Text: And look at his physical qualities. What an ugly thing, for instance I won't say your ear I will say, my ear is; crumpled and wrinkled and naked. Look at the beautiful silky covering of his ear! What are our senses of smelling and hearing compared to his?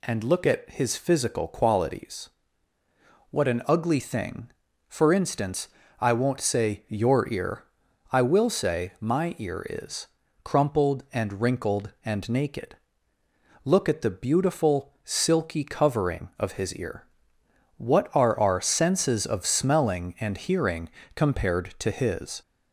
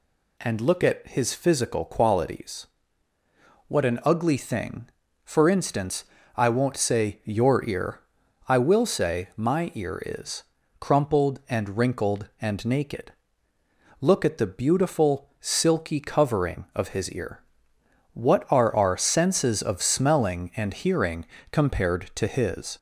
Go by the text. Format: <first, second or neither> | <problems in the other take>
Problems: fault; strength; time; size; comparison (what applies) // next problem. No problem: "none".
neither | pauses between "instance" and "I"; slight; the same in both // pauses between "ear" and "I"; noticeable; the same in both // pauses between "hearing" and "compared"; slight; the same in both